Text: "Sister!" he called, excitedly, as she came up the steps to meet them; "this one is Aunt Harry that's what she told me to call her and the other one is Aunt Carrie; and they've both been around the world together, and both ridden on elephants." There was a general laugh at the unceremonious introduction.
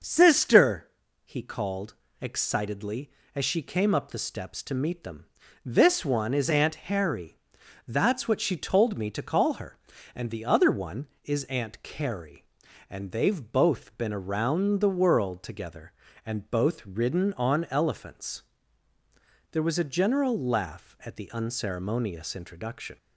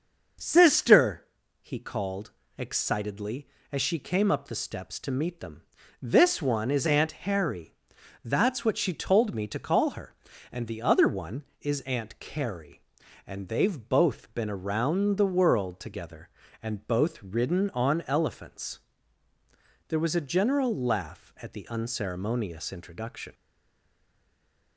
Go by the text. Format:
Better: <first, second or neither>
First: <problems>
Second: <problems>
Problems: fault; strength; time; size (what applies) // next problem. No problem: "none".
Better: first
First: starts louder than the rest; noticeable; until 1.3 s; 6 dB // pauses between "Harry" and "that's"; noticeable; at 7.3 s; 0.50 s long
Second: starts louder than the rest; noticeable; until 1.7 s; 6 dB // pauses between "Harry" and "that's"; noticeable; at 7.7 s; 0.50 s long // stays silent after the last word; noticeable; from 23.3 s on; 1.4 s long